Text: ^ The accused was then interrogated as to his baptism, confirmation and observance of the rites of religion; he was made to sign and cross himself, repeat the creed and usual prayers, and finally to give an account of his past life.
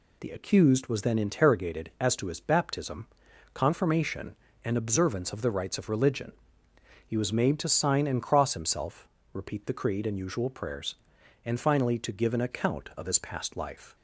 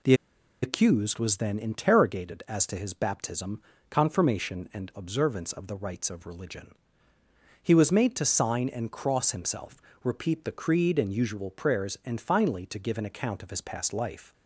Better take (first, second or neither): first